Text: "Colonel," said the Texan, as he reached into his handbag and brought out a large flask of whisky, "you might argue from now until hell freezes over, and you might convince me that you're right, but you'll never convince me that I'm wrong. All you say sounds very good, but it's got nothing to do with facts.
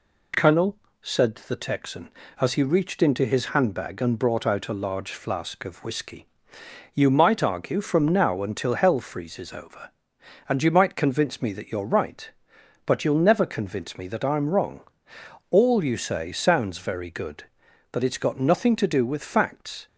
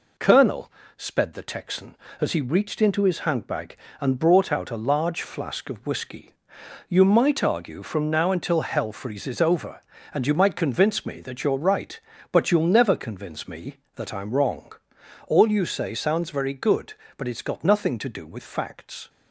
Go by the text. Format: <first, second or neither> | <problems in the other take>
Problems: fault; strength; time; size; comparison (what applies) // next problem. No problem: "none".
first | says "sped" for "said"; at 0.9 s